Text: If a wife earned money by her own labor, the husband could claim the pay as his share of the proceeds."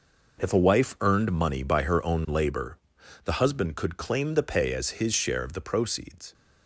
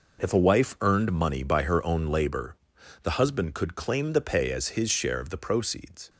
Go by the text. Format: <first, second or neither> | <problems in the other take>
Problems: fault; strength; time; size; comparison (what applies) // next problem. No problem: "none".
neither | none